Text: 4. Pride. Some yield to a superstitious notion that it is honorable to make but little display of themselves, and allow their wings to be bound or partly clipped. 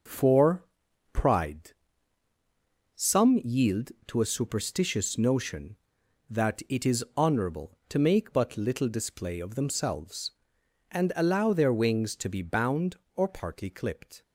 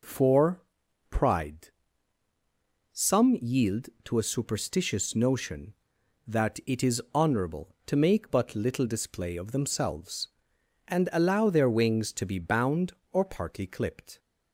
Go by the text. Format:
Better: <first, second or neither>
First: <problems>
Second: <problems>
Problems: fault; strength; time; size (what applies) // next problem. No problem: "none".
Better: second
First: gets quieter; throughout; 6 dB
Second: none